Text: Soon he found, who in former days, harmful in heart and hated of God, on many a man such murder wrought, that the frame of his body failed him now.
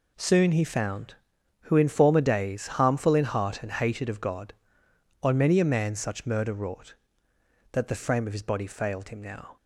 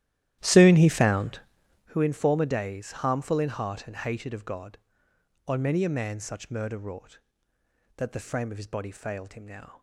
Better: first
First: none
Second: starts louder than the rest; strong; until 1.9 s; 13 dB

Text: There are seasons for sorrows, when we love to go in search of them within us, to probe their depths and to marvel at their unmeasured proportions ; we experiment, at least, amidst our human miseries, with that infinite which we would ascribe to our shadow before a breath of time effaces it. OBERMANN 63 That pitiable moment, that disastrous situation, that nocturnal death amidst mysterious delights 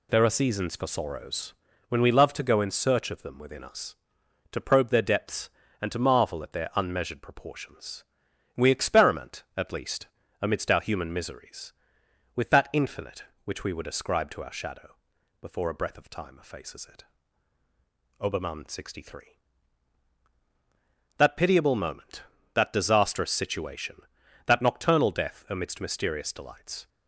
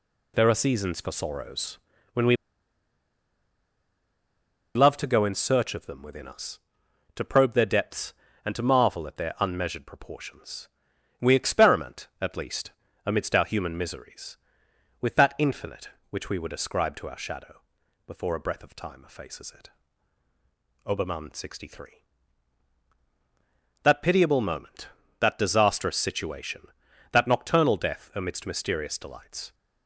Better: first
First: pauses between "shadow" and "before"; noticeable; at 14.9 s; 0.48 s long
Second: pauses between "we" and "love"; strong; at 2.3 s; 2.4 s long // pauses between "shadow" and "before"; noticeable; at 17.5 s; 0.48 s long

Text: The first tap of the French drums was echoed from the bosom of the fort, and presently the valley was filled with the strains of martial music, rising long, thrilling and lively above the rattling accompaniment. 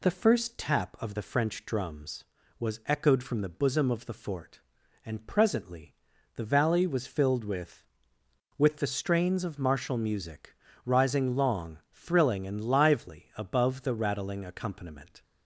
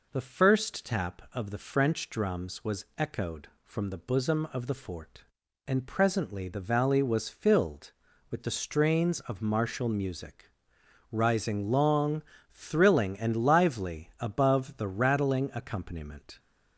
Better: second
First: pauses between "presently" and "the"; at 5.9 s; 0.40 s long // says "with" twice; at 8.5 s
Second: none

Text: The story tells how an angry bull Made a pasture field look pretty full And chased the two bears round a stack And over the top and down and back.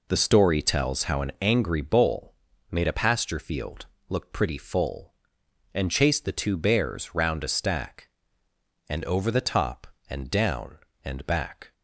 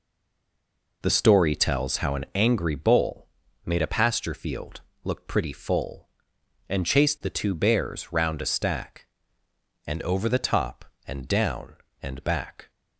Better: first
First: pauses between "bull" and "Made"; at 2.3 s; 0.37 s long // pauses between "field" and "look"; slight; at 3.8 s; 0.22 s long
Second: stays silent before the first word; until 1.0 s; 1.0 s long // pauses between "bull" and "Made"; at 3.2 s; 0.38 s long // pauses between "field" and "look"; slight; at 4.8 s; 0.22 s long

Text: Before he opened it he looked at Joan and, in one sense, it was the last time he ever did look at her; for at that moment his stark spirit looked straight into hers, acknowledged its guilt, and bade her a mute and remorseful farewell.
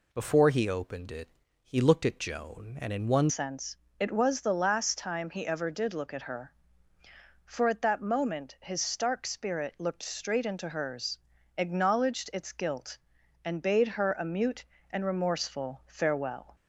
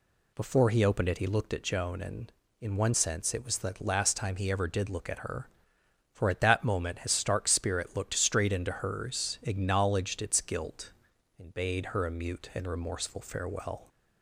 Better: second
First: pauses between "it" and "he"; slight; at 1.2 s; 0.34 s long // changes voice at "sense"; from 3.2 s on; 13.3 s long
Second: none

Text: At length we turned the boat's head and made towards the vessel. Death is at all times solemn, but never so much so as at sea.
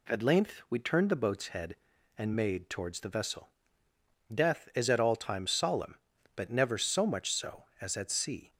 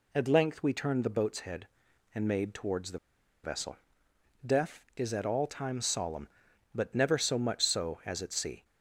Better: first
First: none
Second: pauses between "the" and "vessel"; noticeable; at 2.9 s; 0.46 s long

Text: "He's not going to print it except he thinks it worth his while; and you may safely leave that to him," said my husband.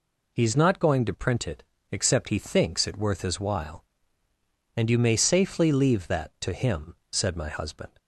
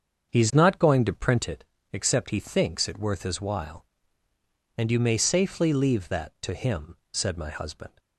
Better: first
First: pauses between "it" and "except"; slight; at 1.6 s; 0.26 s long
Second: starts louder than the rest; until 1.6 s; 7 dB // pauses between "it" and "except"; slight; at 1.6 s; 0.26 s long

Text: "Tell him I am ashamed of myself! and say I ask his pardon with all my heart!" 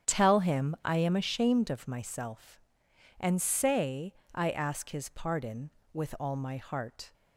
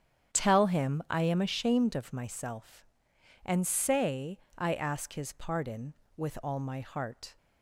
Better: neither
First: starts louder than the rest; strong; until 1.1 s; 8.5 dB // pauses between "say" and "I"; slight; at 4.1 s; 0.22 s long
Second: starts louder than the rest; strong; until 1.4 s; 8.5 dB // pauses between "say" and "I"; slight; at 4.3 s; 0.20 s long

